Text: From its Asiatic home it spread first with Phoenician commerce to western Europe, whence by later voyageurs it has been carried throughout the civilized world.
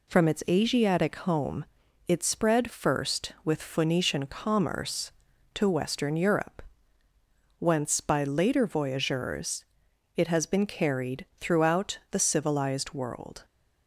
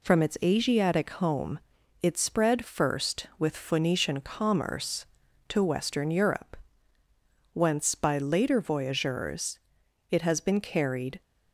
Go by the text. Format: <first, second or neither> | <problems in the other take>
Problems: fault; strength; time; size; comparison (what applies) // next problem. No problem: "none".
first | pauses between "home" and "it"; at 1.6 s; 0.40 s long; also in the first // pauses between "voyageurs" and "it"; noticeable; at 9.5 s; 0.52 s long; noticeable in the first // stops before "throughout the civilized world"; at 11.2 s